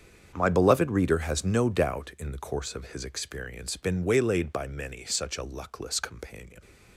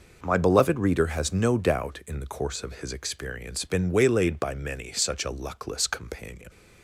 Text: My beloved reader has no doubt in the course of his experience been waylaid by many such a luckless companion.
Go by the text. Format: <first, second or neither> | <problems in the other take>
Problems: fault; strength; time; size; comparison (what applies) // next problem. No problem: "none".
second | gets quieter; strong; throughout; 14 dB